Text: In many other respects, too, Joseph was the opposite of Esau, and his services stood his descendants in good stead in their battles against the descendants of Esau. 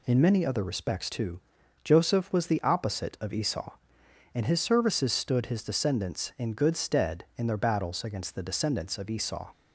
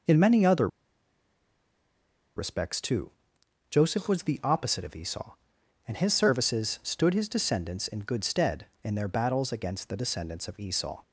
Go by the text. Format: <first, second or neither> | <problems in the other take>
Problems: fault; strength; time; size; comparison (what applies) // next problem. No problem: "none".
first | pauses between "other" and "respects"; strong; at 0.6 s; 1.6 s long